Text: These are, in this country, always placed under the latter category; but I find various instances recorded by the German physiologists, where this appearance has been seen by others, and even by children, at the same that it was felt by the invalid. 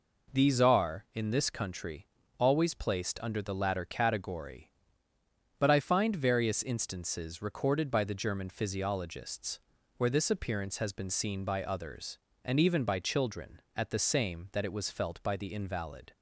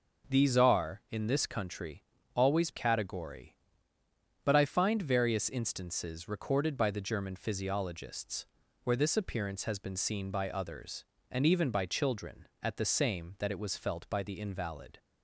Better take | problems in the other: first | skips "placed under the latter"; at 2.7 s

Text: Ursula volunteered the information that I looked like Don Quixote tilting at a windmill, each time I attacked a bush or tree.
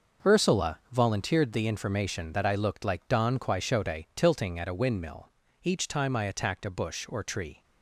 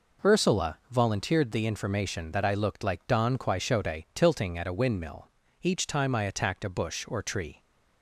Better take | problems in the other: second | gets quieter; strong; throughout; 10 dB

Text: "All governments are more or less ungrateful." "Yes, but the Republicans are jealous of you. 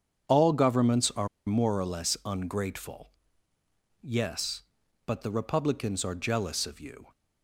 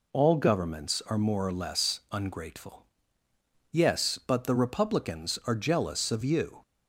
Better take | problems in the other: second | starts louder than the rest; strong; until 1.5 s; 8 dB // pauses between "are" and "more"; slight; at 1.2 s; 0.19 s long

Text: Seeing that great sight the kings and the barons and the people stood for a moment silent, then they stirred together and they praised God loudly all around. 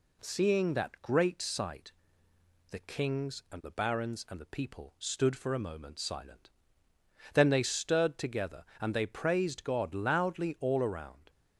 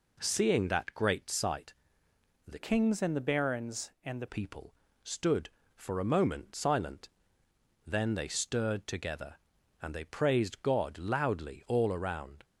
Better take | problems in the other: first | pauses between "sight" and "the"; noticeable; at 1.7 s; 0.70 s long; noticeable in the first // changes voice from "kings" to "the"; from 2.5 to 4.2 s; 1.7 s long // pauses between "people" and "stood"; slight; at 4.7 s; 0.30 s long

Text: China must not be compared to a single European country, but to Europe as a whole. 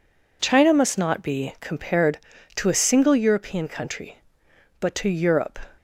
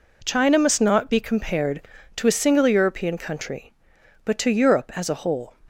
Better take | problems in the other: second | stops before "as a whole"; at 5.7 s

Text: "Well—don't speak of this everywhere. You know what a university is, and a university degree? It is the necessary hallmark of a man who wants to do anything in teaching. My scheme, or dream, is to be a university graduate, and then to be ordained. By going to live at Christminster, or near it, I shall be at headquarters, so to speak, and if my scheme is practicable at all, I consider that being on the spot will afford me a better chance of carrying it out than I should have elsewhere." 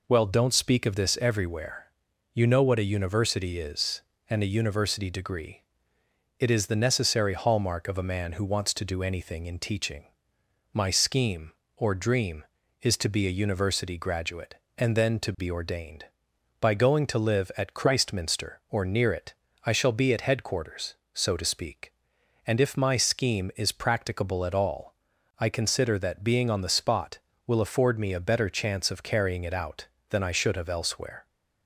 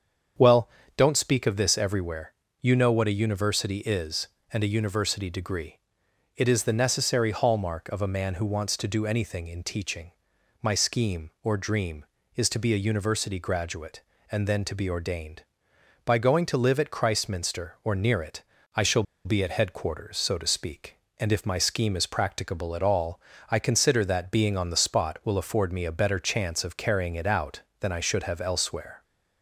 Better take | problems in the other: first | starts louder than the rest; strong; until 1.6 s; 7.5 dB // pauses between "shall" and "be"; slight; at 19.0 s; 0.21 s long

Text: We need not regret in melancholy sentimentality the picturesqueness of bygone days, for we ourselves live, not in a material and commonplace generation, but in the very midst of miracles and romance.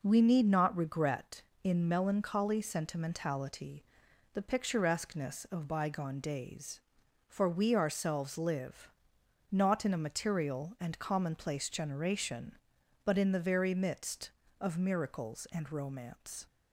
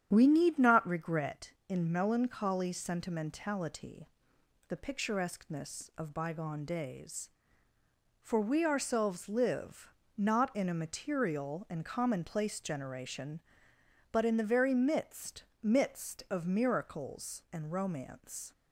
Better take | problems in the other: first | starts louder than the rest; strong; until 1.1 s; 9.5 dB // pauses between "sentimentality" and "the"; noticeable; at 4.0 s; 0.58 s long; noticeable in the first // says "midst" twice; at 15.6 s

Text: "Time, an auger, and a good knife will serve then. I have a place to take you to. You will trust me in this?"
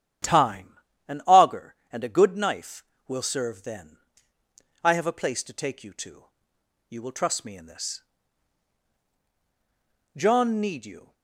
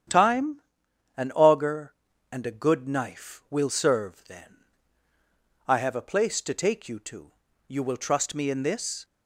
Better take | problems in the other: second | starts louder than the rest; strong; until 1.5 s; 9.5 dB; strong in the second // goes on to say "John need you"; noticeable; from 10.1 s on; 0.98 s long

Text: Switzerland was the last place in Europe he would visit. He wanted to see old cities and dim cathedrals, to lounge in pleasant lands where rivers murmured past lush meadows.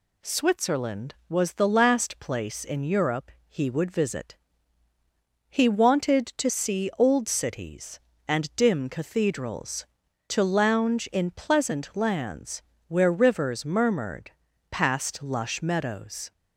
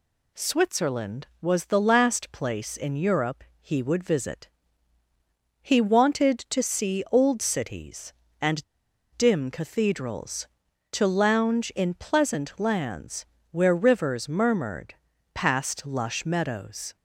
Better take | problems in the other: first | pauses between "Europe" and "he"; slight; at 3.4 s; 0.18 s long; slight in the first // pauses between "and" and "dim"; noticeable; at 8.6 s; 0.54 s long // pauses between "lands" and "where"; slight; at 13.2 s; 0.26 s long; slight in the first // pauses between "murmured" and "past"; at 14.9 s; 0.40 s long; also in the first

